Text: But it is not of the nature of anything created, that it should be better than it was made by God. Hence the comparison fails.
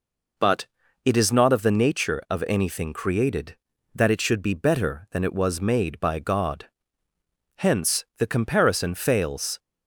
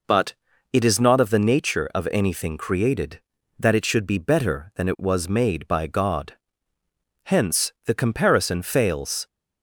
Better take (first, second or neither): neither